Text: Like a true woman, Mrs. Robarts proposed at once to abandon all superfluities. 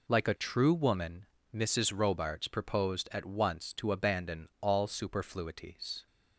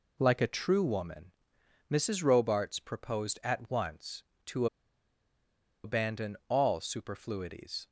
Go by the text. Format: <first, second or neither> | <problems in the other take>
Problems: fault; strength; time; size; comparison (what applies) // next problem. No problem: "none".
first | pauses between "to" and "abandon"; at 4.6 s; 1.1 s long